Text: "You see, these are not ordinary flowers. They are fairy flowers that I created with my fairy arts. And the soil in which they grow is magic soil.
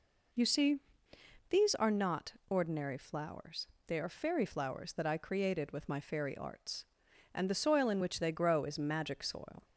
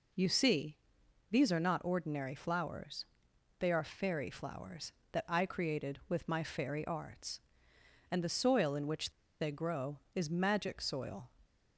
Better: first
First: none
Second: pauses between "which" and "they"; slight; at 9.1 s; 0.29 s long

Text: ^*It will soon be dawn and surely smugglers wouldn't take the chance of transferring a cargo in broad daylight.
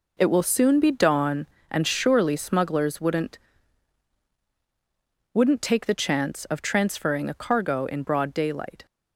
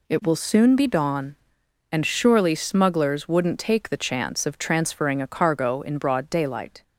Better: second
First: says "wouldn't" twice; at 5.3 s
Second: none

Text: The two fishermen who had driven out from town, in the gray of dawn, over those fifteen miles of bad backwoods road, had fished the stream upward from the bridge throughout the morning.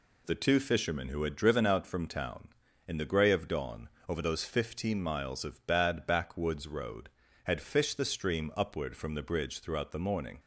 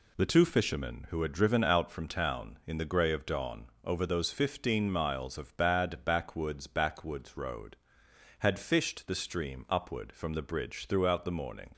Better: first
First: none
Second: says "backwoods" twice; at 6.6 s

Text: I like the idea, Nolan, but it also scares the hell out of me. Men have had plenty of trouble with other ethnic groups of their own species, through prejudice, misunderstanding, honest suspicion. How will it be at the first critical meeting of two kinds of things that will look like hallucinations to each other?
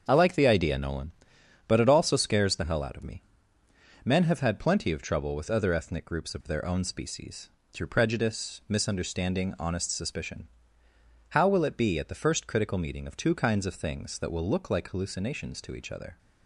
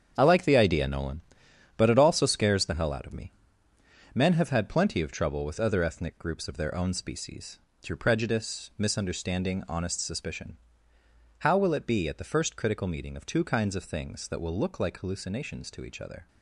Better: first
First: starts louder than the rest; until 1.0 s; 7 dB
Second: gets quieter; strong; throughout; 10 dB // starts louder than the rest; strong; until 1.1 s; 8 dB

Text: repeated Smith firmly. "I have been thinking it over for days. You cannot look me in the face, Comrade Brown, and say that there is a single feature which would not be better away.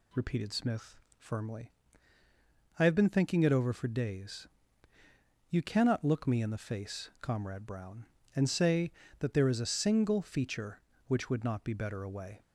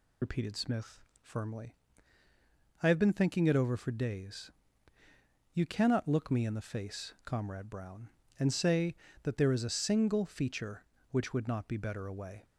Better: first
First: pauses between "Smith" and "firmly"; slight; at 0.9 s; 0.18 s long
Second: loses the start of "repeated"; at 0.2 s; 50 ms // pauses between "Smith" and "firmly"; slight; at 1.0 s; 0.18 s long

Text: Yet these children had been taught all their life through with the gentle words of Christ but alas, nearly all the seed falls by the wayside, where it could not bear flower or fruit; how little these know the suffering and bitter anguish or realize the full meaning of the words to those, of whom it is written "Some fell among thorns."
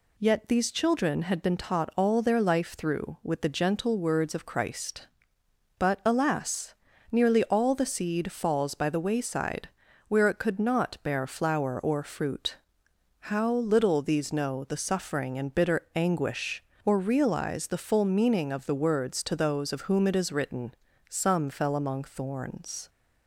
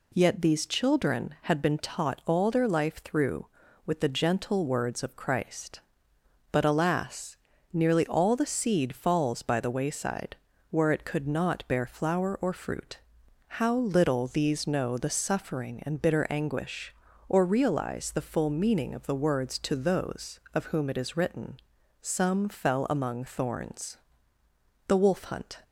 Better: first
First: pauses between "written" and "Some"; slight; at 20.7 s; 0.36 s long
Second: pauses between "written" and "Some"; noticeable; at 21.5 s; 0.46 s long // goes on to say "The wolf hunt"; noticeable; from 24.8 s on; 0.74 s long

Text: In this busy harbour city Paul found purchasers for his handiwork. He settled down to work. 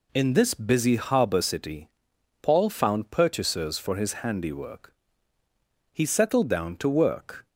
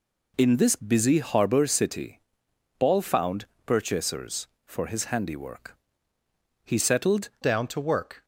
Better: first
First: pauses between "city" and "Paul"; noticeable; at 1.8 s; 0.50 s long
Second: pauses between "city" and "Paul"; noticeable; at 2.1 s; 0.60 s long // pauses between "found" and "purchasers"; slight; at 3.4 s; 0.20 s long // changes voice at "down"; from 7.4 s on; 0.8 s long

